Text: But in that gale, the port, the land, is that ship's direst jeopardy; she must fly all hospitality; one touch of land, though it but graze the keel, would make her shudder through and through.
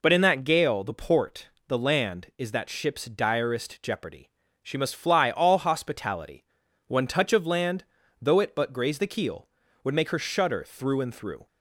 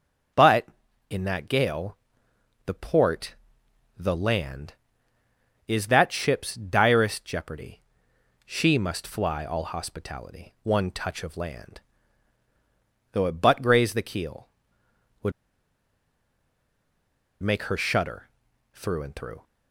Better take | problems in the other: first | starts louder than the rest; until 1.7 s; 7 dB // pauses between "would" and "make"; strong; at 15.3 s; 2.1 s long // pauses between "shudder" and "through"; noticeable; at 18.2 s; 0.46 s long

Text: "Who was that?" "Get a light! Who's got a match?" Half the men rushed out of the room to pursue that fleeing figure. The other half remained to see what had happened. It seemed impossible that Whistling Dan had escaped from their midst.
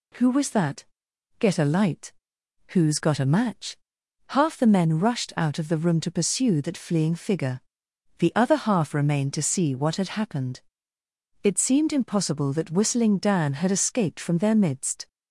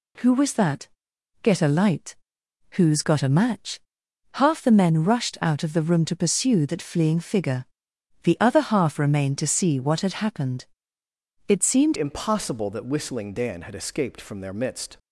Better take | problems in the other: first | changes voice at "impossible"; from 11.9 s on; 3.0 s long

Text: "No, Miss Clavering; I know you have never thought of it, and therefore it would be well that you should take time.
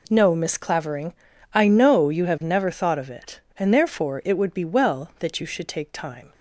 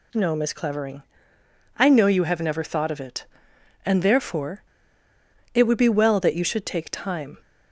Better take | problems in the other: first | pauses between "therefore" and "it"; noticeable; at 4.6 s; 0.89 s long

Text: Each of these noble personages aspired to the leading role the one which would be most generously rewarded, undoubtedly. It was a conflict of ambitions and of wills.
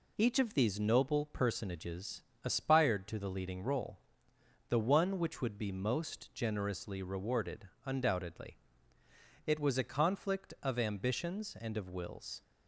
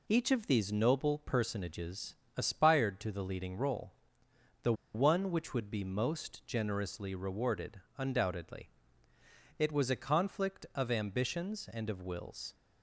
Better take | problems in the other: first | pauses between "personages" and "aspired"; slight; at 2.1 s; 0.22 s long; slight in the first // pauses between "role" and "the"; noticeable; at 3.9 s; 0.70 s long; noticeable in the first // pauses between "the" and "one"; slight; at 4.7 s; 0.20 s long

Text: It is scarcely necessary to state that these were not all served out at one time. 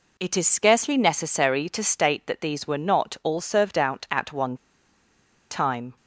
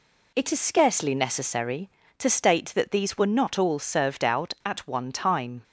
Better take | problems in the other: second | pauses between "one" and "time"; noticeable; at 4.5 s; 0.95 s long

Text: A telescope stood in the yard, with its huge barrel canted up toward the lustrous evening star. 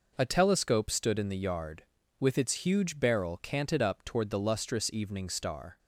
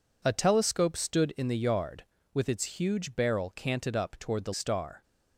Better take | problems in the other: first | skips "lustrous evening"; at 4.5 s

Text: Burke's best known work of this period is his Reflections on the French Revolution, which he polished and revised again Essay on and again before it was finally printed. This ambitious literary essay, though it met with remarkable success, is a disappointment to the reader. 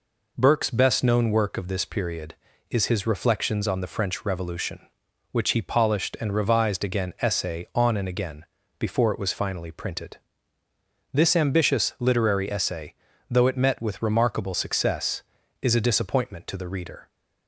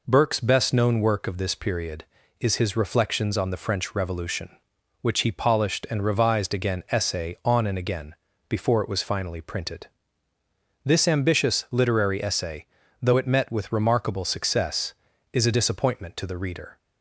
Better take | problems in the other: neither | pauses between "again" and "before"; slight; the same in both

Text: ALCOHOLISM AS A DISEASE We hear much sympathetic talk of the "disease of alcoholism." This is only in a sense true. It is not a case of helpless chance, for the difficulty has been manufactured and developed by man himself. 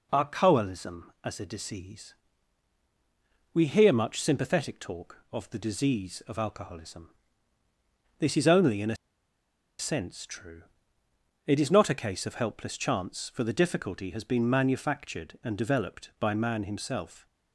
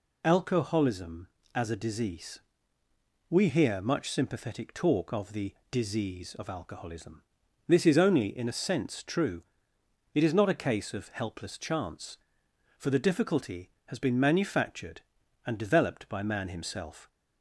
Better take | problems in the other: second | pauses between "DISEASE" and "We"; strong; at 2.1 s; 1.3 s long; noticeable in the second // pauses between "a" and "sense"; noticeable; at 8.9 s; 0.84 s long

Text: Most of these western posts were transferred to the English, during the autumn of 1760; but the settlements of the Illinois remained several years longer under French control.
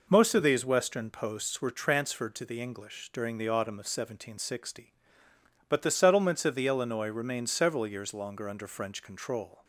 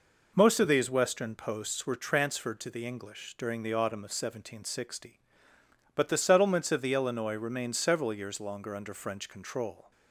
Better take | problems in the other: neither | none

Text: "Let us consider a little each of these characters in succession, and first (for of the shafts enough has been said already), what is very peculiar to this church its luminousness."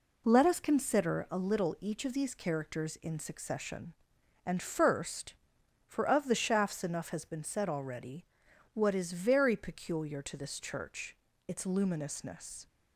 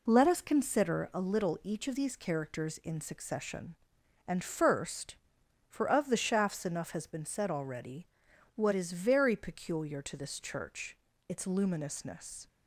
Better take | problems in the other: neither | pauses between "church" and "its"; slight; the same in both

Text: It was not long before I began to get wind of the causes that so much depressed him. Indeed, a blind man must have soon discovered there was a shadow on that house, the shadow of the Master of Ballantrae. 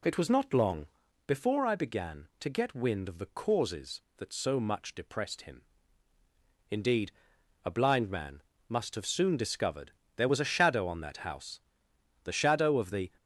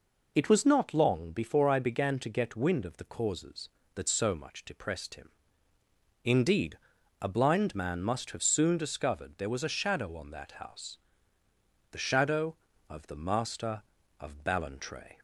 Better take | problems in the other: second | pauses between "long" and "before"; at 0.8 s; 0.38 s long // pauses between "man" and "must"; slight; at 8.4 s; 0.26 s long // pauses between "discovered" and "there"; slight; at 9.9 s; 0.26 s long // stops before "Master of Ballantrae"; at 13.1 s

